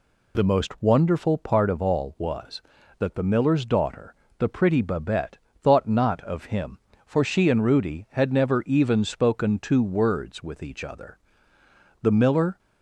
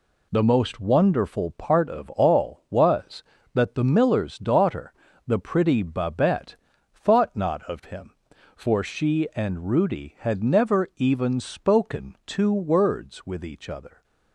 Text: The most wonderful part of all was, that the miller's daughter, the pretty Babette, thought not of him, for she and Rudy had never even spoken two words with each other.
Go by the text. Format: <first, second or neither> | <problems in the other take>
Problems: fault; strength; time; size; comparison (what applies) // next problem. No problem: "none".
second | goes on to say "The miller"; from 12.0 s on; 0.56 s long